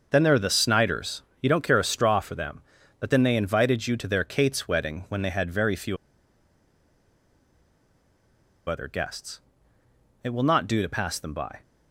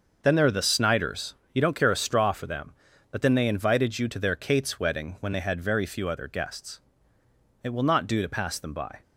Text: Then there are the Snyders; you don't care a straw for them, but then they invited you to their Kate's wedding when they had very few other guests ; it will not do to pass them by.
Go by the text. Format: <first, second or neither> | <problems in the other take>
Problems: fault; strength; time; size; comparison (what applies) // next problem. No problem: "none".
second | starts louder than the rest; noticeable; until 1.1 s; 6 dB; noticeable in the second // pauses between "few" and "other"; strong; at 5.9 s; 2.7 s long